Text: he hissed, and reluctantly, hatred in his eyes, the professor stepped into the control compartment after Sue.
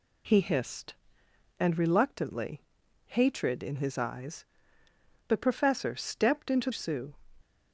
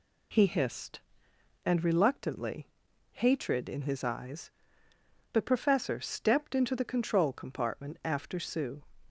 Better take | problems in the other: second | skips "the control compartment after"; at 6.6 s

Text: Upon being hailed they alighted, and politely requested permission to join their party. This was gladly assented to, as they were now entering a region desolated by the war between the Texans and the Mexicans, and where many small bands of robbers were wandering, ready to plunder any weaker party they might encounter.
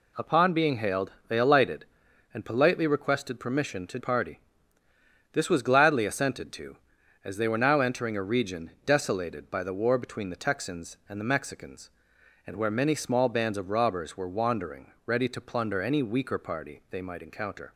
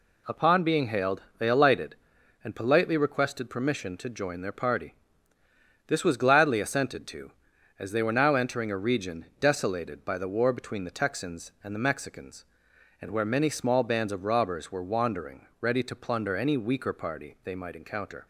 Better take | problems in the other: second | pauses between "hailed" and "they"; slight; at 1.1 s; 0.16 s long; slight in the second // skips "join their"; at 3.9 s

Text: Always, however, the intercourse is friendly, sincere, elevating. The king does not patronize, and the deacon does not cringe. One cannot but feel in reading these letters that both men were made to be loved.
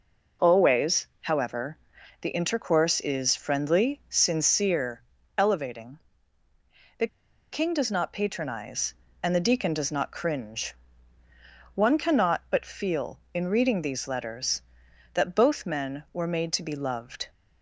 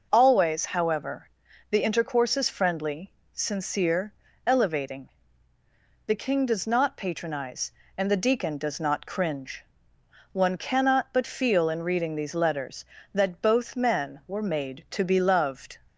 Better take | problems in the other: second | pauses between "The" and "king"; at 7.0 s; 0.45 s long

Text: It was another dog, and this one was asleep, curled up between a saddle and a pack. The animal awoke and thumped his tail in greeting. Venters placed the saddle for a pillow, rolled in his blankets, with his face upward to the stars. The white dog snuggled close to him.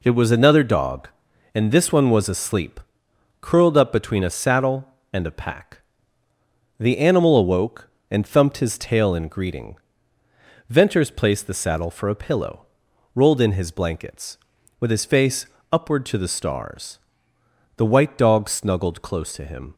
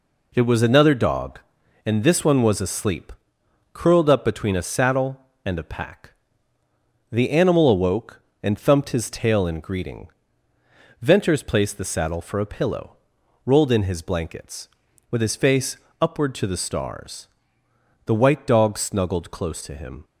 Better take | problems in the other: neither | pauses between "face" and "upward"; slight; the same in both

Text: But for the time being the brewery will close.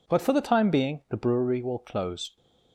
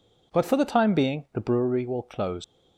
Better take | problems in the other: first | leaves "close" unfinished; at 2.4 s; 150 ms

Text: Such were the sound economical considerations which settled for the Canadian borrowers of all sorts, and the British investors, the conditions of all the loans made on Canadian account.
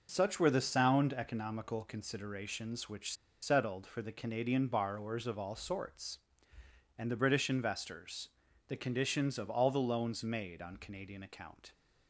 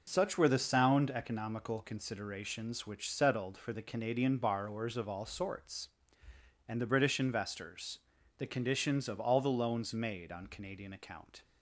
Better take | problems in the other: second | pauses between "which" and "settled"; slight; at 3.1 s; 0.28 s long

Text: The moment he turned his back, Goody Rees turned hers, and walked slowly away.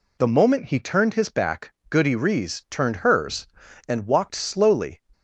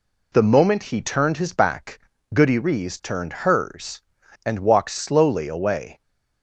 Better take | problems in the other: second | stops before "away"; at 5.1 s

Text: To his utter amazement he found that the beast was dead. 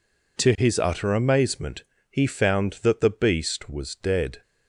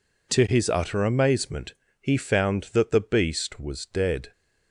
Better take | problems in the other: neither | pauses between "amazement" and "he"; slight; the same in both

